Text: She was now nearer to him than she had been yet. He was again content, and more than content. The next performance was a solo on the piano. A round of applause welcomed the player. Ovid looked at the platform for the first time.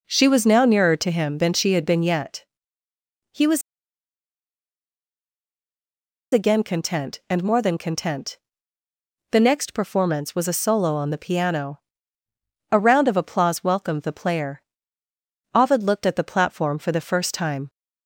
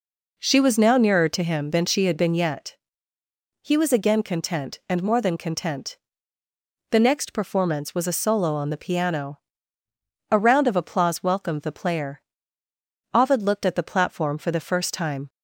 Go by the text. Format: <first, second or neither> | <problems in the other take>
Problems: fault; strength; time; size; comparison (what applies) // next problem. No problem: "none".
second | pauses between "was" and "again"; strong; at 3.6 s; 2.7 s long